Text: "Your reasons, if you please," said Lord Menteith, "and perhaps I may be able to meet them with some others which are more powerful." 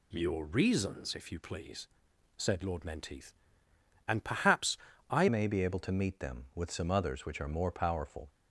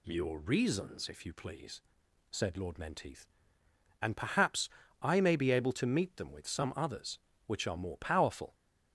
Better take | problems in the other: second | pauses between "perhaps" and "I"; slight; at 4.7 s; 0.34 s long; slight in the second // changes voice at "may"; from 5.2 s on; 3.0 s long

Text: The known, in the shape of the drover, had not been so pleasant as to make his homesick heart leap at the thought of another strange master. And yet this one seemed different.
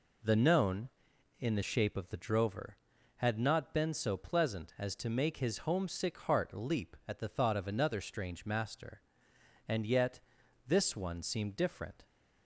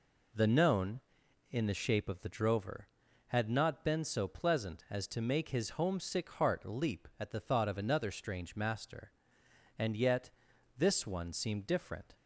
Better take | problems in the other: neither | pauses between "yet" and "this"; noticeable; the same in both

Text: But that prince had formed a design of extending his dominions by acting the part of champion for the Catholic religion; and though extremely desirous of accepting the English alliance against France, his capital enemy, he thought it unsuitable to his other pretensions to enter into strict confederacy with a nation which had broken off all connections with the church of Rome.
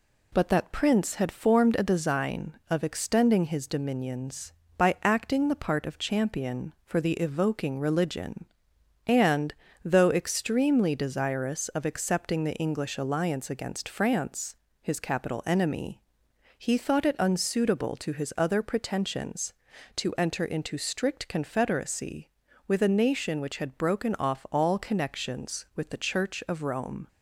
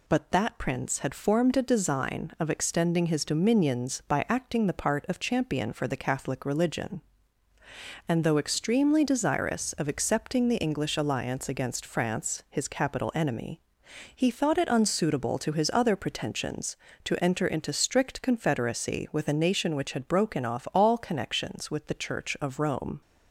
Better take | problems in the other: second | says "Evoking" for "Catholic"; at 7.1 s // pauses between "and" and "though"; slight; at 9.5 s; 0.30 s long

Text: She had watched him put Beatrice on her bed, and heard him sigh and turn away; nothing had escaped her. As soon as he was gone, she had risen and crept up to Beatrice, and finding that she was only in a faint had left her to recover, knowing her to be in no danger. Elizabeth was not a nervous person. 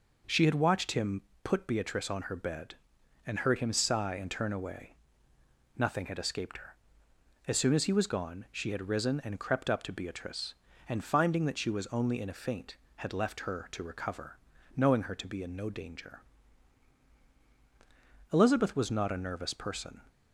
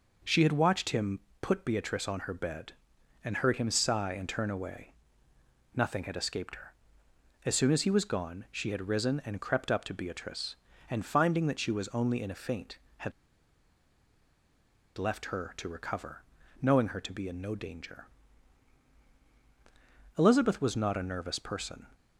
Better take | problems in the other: first | pauses between "him" and "put"; slight; at 1.1 s; 0.22 s long; slight in the first // pauses between "had" and "left"; strong; at 13.1 s; 1.8 s long

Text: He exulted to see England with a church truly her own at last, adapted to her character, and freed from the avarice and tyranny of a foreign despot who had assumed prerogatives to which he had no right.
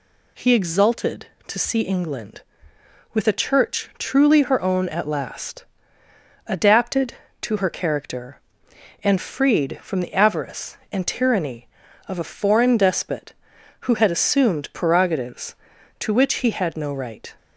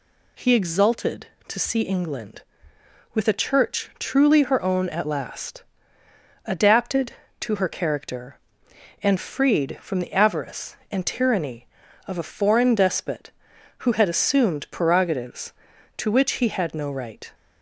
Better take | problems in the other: neither | none

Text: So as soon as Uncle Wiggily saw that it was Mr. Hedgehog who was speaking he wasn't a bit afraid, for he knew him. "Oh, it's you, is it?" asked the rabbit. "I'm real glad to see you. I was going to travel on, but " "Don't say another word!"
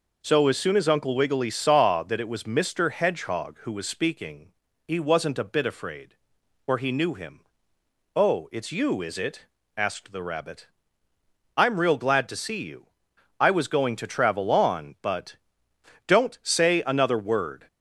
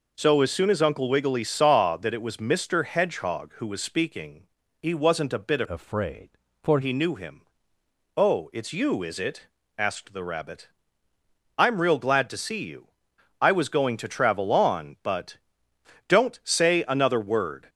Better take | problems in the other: first | pauses between "speaking" and "he"; slight; at 4.4 s; 0.36 s long; slight in the first // changes voice from "afraid" to "for"; from 5.7 to 6.8 s; 1.1 s long

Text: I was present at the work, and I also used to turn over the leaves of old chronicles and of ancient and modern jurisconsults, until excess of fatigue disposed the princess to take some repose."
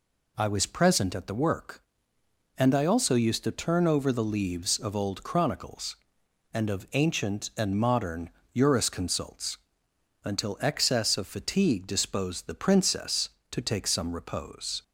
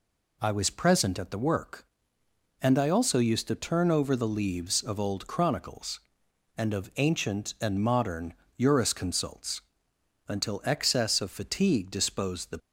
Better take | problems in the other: first | pauses between "modern" and "jurisconsults"; slight; at 8.3 s; 0.24 s long; slight in the first // stops before "princess to take some repose"; at 12.5 s

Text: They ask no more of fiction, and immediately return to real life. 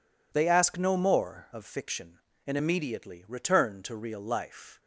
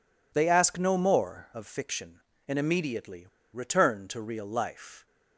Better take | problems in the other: first | pauses between "immediately" and "return"; slight; at 3.2 s; 0.26 s long

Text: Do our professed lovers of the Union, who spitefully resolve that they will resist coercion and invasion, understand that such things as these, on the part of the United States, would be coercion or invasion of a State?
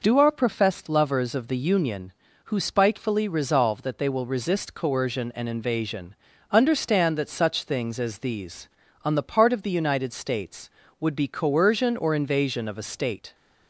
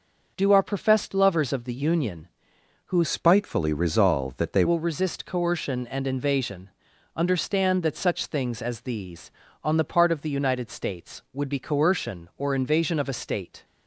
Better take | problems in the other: first | changes voice from "spitefully" to "they"; from 3.0 to 4.6 s; 1.6 s long

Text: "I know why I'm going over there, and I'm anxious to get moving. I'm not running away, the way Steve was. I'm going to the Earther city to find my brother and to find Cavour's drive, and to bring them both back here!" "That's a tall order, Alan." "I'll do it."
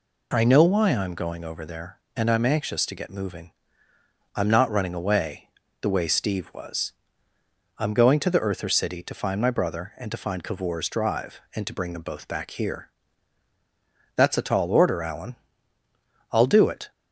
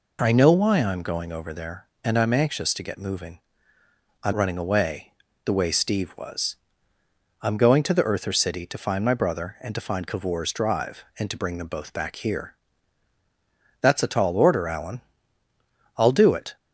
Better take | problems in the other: first | skips "not"; at 4.3 s

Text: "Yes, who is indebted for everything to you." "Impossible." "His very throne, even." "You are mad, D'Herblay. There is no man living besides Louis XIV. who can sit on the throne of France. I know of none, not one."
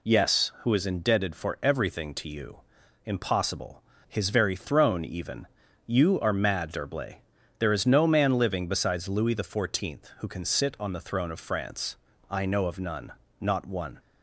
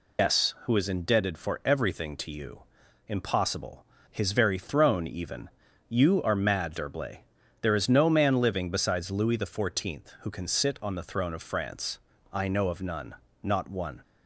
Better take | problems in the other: first | loses the start of "Yes"; at 0.1 s; 135 ms

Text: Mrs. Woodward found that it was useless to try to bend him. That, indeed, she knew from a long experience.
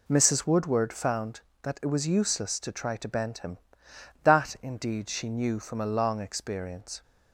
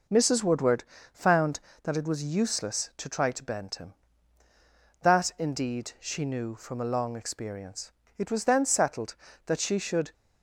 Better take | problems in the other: first | pauses between "Woodward" and "found"; slight; at 0.8 s; 0.30 s long // goes on to say "It was then settled that she should"; strong; from 8.1 s on; 1.9 s long

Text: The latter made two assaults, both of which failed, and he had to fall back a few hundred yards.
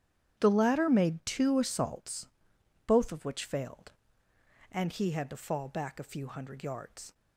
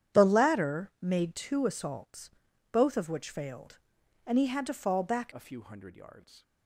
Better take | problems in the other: first | starts louder than the rest; strong; until 1.2 s; 9.5 dB; strong in the first // changes voice at "a"; from 5.3 s on; 1.1 s long

